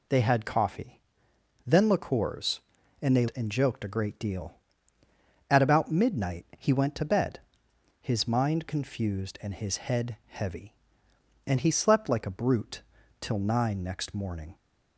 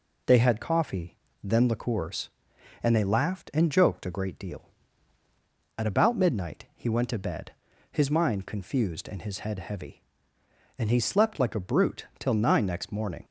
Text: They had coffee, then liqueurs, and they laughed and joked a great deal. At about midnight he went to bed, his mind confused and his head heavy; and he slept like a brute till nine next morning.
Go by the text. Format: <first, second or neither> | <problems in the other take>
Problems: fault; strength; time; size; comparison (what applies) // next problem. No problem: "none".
second | skips "laughed"; at 3.3 s // pauses between "brute" and "till"; slight; at 12.8 s; 0.36 s long